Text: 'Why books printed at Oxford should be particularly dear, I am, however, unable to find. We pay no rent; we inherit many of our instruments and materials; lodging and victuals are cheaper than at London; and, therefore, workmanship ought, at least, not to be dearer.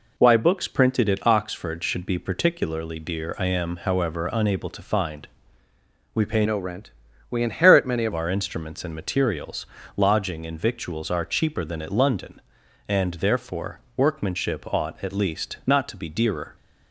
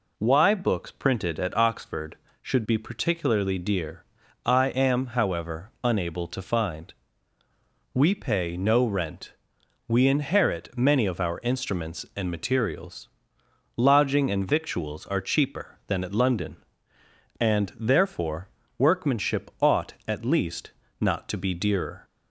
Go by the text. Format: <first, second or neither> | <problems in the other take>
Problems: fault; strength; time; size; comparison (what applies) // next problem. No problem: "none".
second | changes voice from "no" to "of"; from 6.4 to 8.1 s; 1.7 s long